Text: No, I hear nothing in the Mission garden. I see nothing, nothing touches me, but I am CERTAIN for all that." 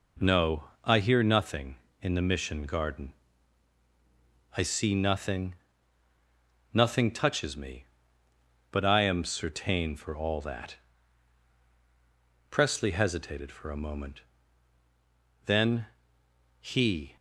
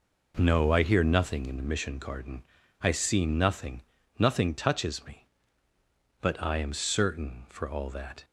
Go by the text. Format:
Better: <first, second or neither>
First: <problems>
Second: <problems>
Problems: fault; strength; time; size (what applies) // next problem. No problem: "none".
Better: second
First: goes on to say "Presley hesitated for a moment then he"; strong; from 12.4 s on; 4.6 s long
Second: none